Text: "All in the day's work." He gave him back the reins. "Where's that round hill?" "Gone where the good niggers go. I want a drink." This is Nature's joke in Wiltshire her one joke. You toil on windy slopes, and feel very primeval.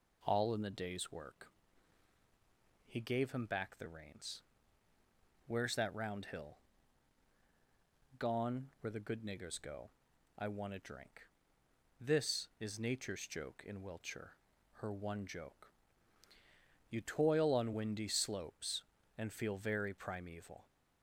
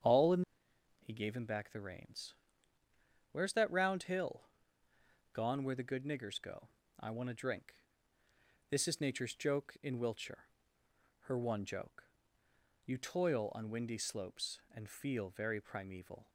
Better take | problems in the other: first | starts louder than the rest; strong; until 1.6 s; 8 dB // skips "the day's work"; at 0.7 s // pauses between "Wiltshire" and "her"; noticeable; at 10.4 s; 0.76 s long; also in the first

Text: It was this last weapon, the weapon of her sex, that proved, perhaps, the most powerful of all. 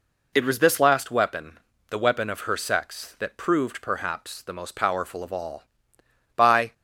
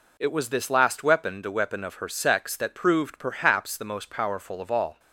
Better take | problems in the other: second | goes on to say "By"; slight; from 6.3 s on; 0.38 s long

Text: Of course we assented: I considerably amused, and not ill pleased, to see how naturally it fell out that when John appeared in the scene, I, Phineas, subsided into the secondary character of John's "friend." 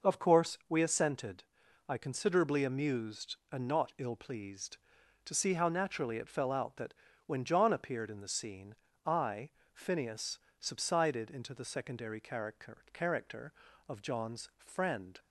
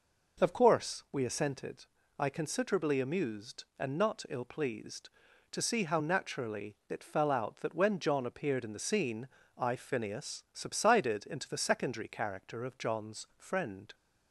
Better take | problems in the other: second | pauses between "that" and "when"; slight; at 6.9 s; 0.32 s long // says "character" twice; at 12.9 s

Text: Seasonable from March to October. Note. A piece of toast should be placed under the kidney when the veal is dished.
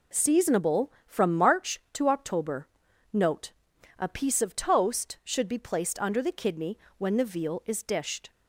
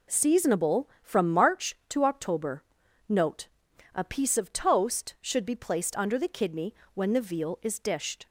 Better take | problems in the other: neither | pauses between "kidney" and "when"; slight; the same in both

